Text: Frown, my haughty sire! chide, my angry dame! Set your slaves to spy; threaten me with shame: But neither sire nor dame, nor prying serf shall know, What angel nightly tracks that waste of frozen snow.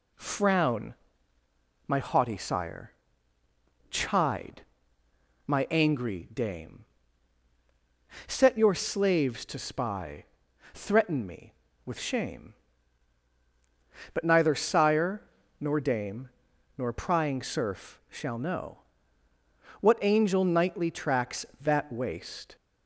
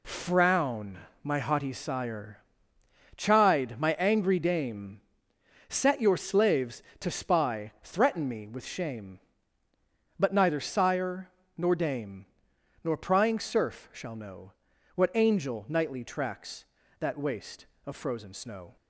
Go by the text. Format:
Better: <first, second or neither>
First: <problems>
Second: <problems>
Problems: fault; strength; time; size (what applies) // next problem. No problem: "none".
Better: second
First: pauses between "sire" and "nor"; at 15.2 s; 0.38 s long // stops before "of frozen snow"; at 22.5 s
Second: pauses between "sire" and "nor"; slight; at 11.3 s; 0.26 s long